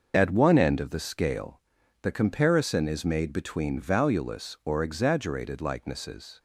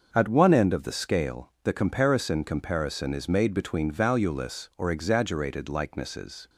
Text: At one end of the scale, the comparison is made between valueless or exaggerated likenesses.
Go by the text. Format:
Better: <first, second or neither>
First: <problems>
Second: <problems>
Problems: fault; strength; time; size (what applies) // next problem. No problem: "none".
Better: first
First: starts louder than the rest; noticeable; until 1.1 s; 6 dB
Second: starts louder than the rest; until 1.1 s; 6.5 dB // says "comparison" twice; at 2.4 s